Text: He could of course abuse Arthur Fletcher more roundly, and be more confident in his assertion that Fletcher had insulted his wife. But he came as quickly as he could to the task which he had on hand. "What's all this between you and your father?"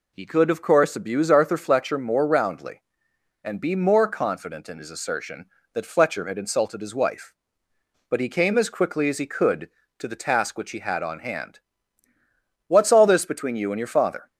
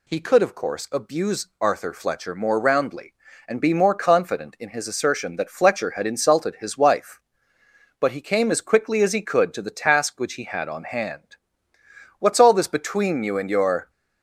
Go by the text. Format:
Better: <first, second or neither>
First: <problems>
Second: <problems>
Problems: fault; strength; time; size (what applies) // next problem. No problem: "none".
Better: first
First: none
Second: stops before "father"; at 13.8 s